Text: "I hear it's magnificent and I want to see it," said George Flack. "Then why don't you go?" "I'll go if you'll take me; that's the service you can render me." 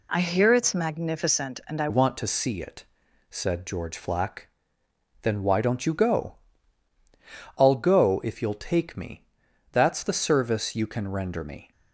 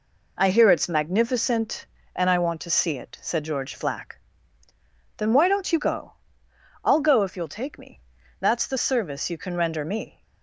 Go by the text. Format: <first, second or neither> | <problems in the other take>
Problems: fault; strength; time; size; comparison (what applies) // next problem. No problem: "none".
second | changes voice at "want"; from 1.8 s on; 9.9 s long